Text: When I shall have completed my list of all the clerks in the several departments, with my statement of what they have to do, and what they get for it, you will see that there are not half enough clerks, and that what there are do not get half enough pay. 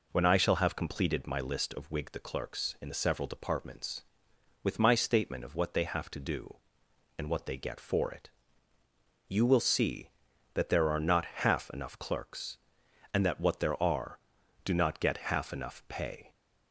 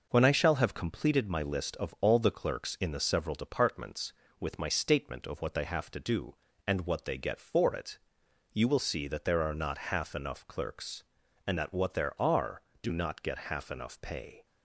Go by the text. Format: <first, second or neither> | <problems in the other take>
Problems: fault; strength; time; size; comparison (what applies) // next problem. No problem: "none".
second | says "whig" for "all"; at 1.9 s